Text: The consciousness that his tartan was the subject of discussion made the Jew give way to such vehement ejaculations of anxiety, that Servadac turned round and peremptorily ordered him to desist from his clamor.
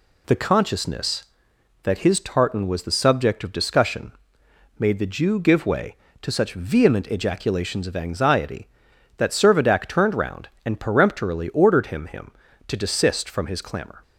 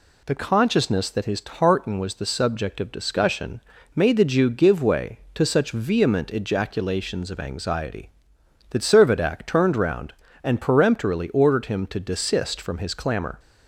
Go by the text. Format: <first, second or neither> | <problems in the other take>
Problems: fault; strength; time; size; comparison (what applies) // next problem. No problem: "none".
second | pauses between "discussion" and "made"; noticeable; at 4.1 s; 0.68 s long; slight in the second // says "him" twice; at 12.0 s